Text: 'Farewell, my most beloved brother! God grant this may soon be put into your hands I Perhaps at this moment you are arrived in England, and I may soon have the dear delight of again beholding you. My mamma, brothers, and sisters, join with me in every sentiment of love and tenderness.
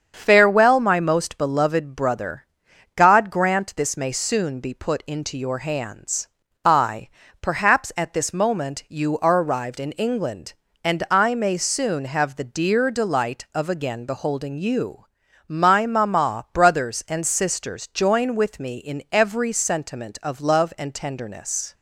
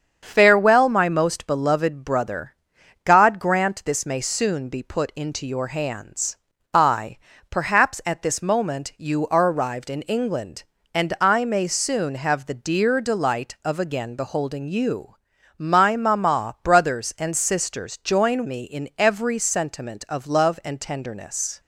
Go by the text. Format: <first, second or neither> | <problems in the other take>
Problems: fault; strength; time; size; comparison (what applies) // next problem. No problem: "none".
first | starts louder than the rest; strong; until 1.2 s; 7 dB; strong in the first // pauses between "hands" and "I"; slight; at 6.3 s; 0.36 s long; slight in the first // pauses between "I" and "Perhaps"; slight; at 7.1 s; 0.32 s long; slight in the first // skips "with"; at 18.4 s